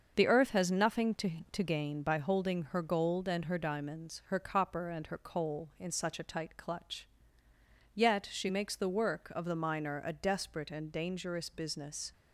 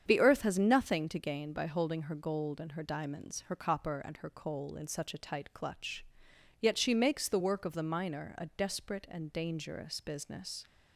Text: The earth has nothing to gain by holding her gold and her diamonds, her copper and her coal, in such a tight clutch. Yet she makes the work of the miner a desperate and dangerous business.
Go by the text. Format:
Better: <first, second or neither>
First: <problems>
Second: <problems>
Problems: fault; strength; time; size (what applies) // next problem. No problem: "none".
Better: second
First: starts louder than the rest; until 1.1 s; 6.5 dB // says "to" twice; at 1.5 s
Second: starts louder than the rest; strong; until 1.0 s; 8 dB